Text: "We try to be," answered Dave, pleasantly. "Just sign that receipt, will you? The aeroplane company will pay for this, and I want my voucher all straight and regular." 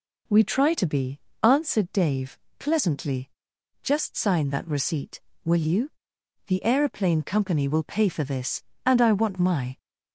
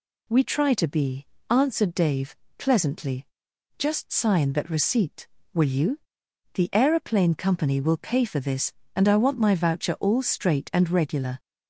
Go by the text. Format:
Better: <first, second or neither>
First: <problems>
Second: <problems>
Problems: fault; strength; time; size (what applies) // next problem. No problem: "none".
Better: second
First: stops before "voucher all straight and regular"; at 9.7 s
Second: none